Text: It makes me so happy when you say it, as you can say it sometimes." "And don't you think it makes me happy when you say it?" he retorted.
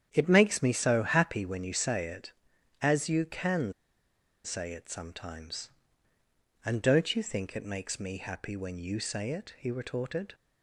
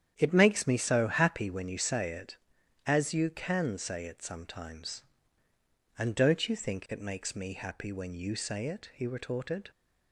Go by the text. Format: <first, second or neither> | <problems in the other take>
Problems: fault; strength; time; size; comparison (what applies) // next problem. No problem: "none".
second | starts louder than the rest; strong; until 1.1 s; 9 dB; strong in the second // pauses between "can" and "say"; noticeable; at 3.7 s; 0.72 s long